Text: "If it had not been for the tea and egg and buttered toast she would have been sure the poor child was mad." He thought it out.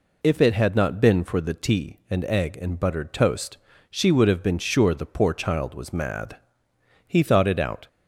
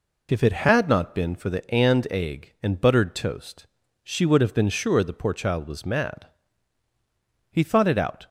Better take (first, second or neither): first